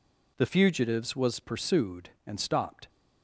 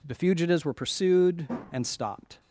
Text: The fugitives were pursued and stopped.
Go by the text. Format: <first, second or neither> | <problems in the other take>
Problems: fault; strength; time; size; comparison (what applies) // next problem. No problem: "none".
second | says "was" for "were"; at 1.1 s